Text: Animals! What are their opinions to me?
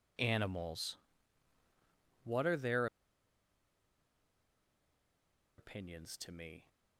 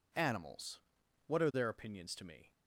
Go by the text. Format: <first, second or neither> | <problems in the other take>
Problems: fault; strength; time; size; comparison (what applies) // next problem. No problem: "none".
second | pauses between "their" and "opinions"; strong; at 2.8 s; 2.7 s long